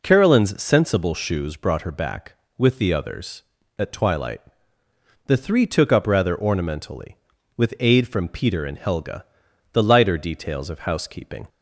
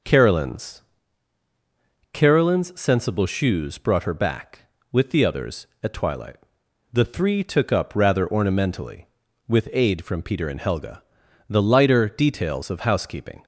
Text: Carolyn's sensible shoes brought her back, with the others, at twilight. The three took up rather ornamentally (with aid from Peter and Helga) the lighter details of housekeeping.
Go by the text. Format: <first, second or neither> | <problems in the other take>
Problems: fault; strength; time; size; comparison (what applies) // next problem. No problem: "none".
first | says "Carolyn's" twice; at 2.1 s